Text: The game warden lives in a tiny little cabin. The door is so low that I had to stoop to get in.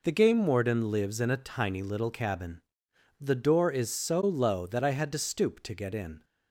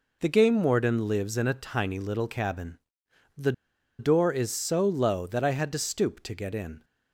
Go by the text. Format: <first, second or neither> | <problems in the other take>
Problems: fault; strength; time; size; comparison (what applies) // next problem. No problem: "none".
first | pauses between "The" and "door"; noticeable; at 3.5 s; 0.47 s long